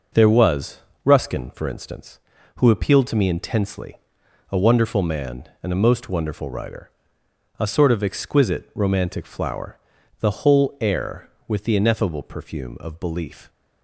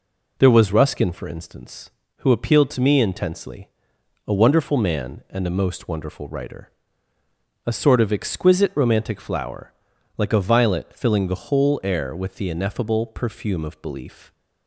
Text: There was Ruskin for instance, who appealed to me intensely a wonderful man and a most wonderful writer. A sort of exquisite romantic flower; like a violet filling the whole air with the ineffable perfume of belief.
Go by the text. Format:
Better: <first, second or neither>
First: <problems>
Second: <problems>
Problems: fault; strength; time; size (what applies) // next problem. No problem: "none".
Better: second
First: pauses between "was" and "Ruskin"; slight; at 0.7 s; 0.26 s long // pauses between "intensely" and "a"; noticeable; at 3.9 s; 0.54 s long // skips "like a violet filling"; at 9.9 s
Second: pauses between "intensely" and "a"; noticeable; at 3.6 s; 0.58 s long